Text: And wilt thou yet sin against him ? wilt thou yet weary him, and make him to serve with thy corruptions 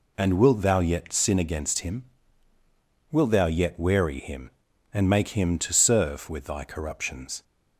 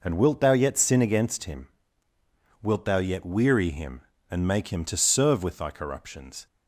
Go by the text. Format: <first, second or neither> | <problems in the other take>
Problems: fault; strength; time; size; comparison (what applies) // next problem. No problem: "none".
neither | none